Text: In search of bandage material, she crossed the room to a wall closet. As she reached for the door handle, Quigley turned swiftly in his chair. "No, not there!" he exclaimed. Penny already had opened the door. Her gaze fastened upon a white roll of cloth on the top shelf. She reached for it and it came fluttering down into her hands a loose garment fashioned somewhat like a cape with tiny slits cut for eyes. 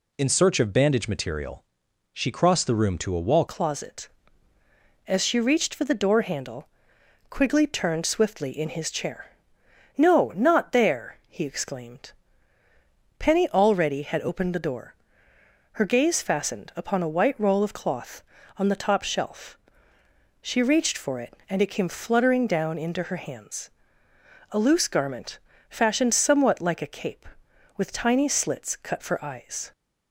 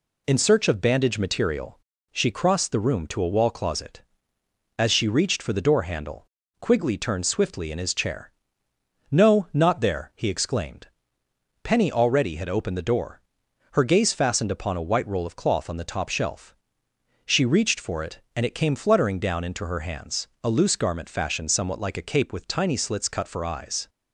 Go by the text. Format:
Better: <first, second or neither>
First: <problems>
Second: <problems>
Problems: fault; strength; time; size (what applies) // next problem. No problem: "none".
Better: second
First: changes voice at "closet"; from 3.4 s on; 26.3 s long // pauses between "hands" and "a"; noticeable; at 23.6 s; 0.80 s long // pauses between "garment" and "fashioned"; slight; at 25.3 s; 0.32 s long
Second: none